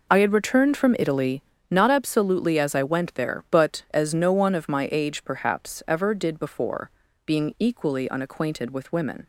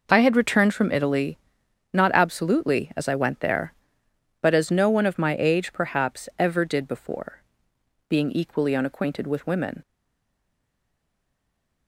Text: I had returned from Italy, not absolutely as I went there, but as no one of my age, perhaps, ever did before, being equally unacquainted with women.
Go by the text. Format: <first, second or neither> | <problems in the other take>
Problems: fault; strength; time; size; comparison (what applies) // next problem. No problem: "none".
first | stays silent after the last word; noticeable; from 9.8 s on; 2.0 s long